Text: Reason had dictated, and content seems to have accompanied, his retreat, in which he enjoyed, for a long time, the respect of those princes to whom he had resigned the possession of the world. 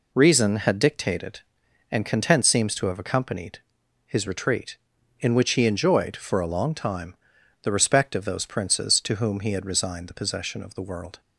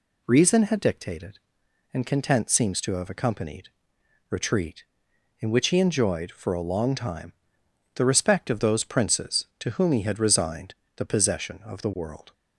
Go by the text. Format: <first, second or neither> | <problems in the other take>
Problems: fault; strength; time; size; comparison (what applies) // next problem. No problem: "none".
first | skips "his"; at 3.9 s // pauses between "resigned" and "the"; slight; at 10.7 s; 0.20 s long